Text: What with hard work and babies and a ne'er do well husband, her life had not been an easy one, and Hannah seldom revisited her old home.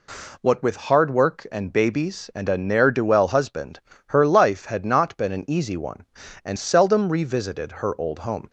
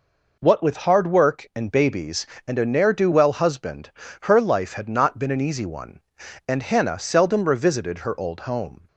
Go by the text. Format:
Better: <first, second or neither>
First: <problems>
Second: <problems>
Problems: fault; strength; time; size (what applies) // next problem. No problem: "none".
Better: second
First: skips "Hannah"; at 6.5 s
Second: none